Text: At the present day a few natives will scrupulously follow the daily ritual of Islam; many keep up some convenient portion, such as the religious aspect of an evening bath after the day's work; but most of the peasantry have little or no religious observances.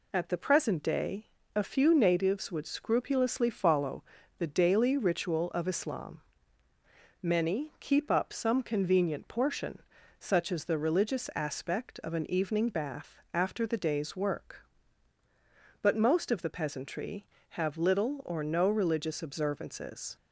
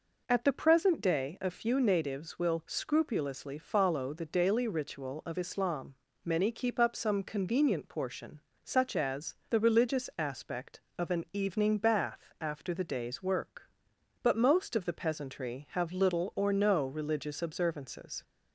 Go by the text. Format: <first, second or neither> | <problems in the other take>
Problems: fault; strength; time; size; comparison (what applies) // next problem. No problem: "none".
second | pauses between "day" and "a"; slight; at 1.2 s; 0.28 s long // says "would" for "will"; at 2.5 s // pauses between "follow" and "the"; slight; at 4.0 s; 0.36 s long // pauses between "bath" and "after"; slight; at 13.1 s; 0.16 s long